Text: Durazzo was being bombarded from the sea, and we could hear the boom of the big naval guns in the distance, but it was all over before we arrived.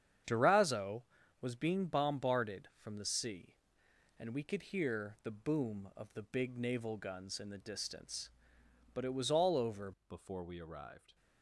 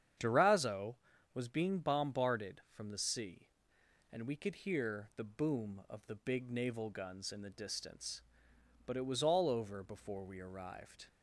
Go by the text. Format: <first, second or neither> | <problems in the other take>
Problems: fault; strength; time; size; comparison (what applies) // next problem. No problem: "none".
second | starts louder than the rest; strong; until 1.6 s; 8 dB; strong in the second // changes voice at "before"; from 10.0 s on; 1.1 s long